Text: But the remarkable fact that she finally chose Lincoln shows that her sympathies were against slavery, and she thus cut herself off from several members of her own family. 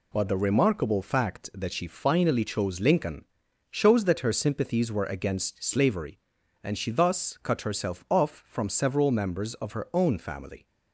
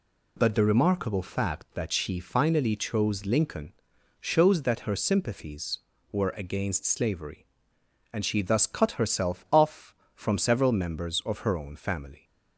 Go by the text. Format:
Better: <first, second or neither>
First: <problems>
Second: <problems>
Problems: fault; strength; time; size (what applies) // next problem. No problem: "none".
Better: neither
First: pauses between "Lincoln" and "shows"; noticeable; at 3.2 s; 0.46 s long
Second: pauses between "Lincoln" and "shows"; noticeable; at 3.7 s; 0.48 s long